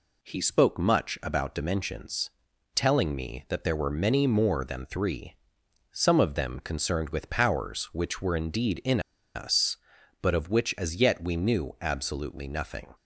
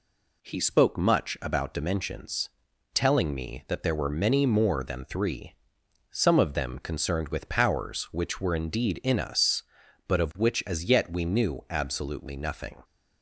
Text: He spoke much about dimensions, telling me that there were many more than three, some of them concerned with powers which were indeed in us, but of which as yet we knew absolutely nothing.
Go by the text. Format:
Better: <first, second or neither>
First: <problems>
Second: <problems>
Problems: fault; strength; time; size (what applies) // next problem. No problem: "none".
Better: second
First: pauses between "in" and "us"; slight; at 8.9 s; 0.35 s long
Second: none